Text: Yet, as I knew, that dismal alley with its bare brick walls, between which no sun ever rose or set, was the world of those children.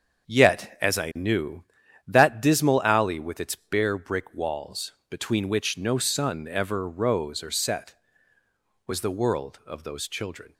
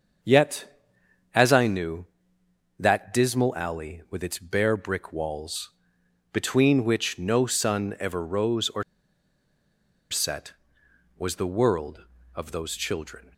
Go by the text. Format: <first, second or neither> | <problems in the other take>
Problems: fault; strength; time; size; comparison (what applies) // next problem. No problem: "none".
first | starts louder than the rest; until 1.7 s; 6.5 dB; also in the first // pauses between "or" and "set"; strong; at 8.8 s; 1.2 s long